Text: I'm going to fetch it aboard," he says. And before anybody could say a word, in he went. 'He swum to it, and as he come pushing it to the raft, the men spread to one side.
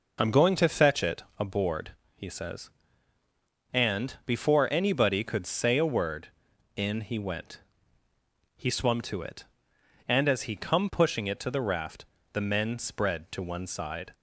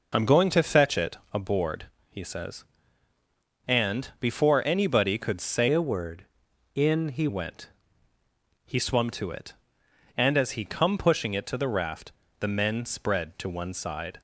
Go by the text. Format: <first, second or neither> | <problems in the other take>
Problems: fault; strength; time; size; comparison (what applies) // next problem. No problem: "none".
first | pauses between "it" and "aboard"; slight; at 1.1 s; 0.16 s long; slight in the first // changes voice from "a" to "he"; from 5.7 to 7.2 s; 1.5 s long